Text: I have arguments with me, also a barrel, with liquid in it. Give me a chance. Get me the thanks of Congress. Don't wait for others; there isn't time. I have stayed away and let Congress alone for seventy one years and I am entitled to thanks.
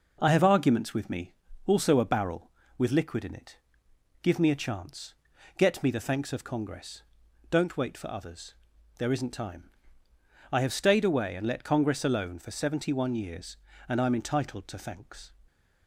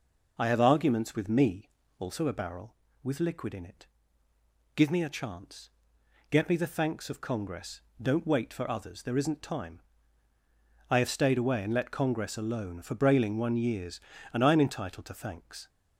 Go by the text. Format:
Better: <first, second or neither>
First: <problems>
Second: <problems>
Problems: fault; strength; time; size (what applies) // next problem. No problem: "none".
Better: first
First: none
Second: says "brailing" for "seventy"; at 12.9 s